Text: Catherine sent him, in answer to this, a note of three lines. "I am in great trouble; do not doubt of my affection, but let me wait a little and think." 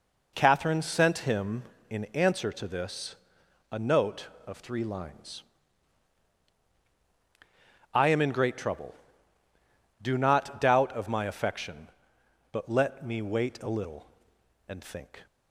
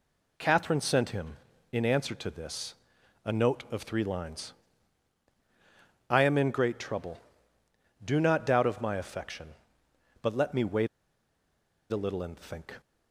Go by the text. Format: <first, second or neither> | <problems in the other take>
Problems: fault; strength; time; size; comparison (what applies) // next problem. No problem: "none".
first | pauses between "wait" and "a"; at 10.8 s; 1.0 s long